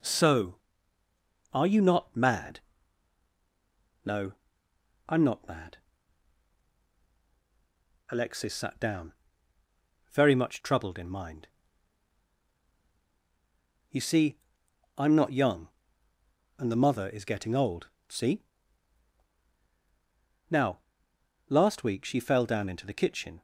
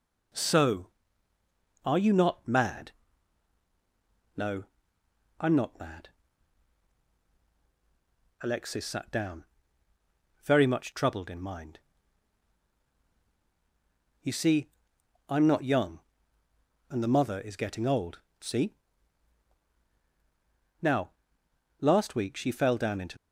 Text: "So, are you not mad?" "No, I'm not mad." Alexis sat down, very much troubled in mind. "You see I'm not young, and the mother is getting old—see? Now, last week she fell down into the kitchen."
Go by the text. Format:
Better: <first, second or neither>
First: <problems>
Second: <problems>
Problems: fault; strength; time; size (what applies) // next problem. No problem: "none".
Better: first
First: pauses between "see" and "I'm"; noticeable; at 14.3 s; 0.58 s long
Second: pauses between "see" and "I'm"; noticeable; at 14.7 s; 0.58 s long // stops before "the kitchen"; at 23.1 s